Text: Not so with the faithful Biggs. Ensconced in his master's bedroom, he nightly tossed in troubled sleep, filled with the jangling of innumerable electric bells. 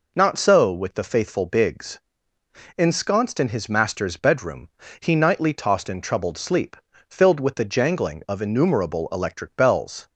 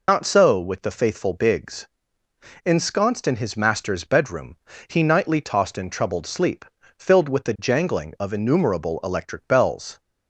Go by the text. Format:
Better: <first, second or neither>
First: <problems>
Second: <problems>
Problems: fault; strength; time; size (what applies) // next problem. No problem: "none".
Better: first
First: none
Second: loses the start of "Not"; at 0.0 s; 45 ms